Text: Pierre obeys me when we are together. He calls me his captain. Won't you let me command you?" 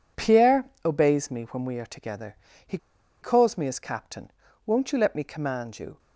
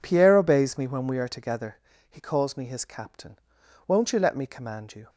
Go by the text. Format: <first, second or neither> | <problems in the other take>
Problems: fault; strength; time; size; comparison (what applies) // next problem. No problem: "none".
second | pauses between "Pierre" and "obeys"; slight; at 0.6 s; 0.22 s long // pauses between "He" and "calls"; at 2.7 s; 0.44 s long